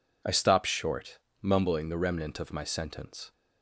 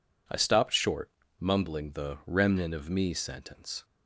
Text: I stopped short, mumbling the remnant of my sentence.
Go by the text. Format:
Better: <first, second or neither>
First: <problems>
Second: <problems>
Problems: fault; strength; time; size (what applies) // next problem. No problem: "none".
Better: first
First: none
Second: says "me" for "my"; at 2.9 s